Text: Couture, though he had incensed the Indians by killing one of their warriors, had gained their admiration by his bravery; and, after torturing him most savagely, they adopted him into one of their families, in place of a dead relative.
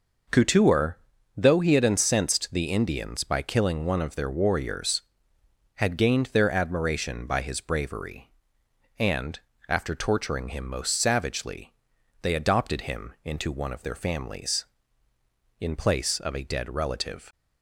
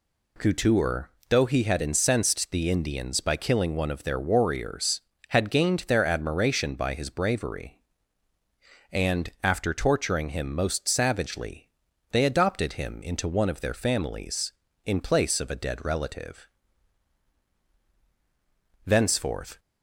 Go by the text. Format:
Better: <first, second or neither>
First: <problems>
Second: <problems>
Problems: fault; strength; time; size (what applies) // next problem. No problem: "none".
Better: first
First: none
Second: goes on to say "Thenceforth"; noticeable; from 18.8 s on; 0.74 s long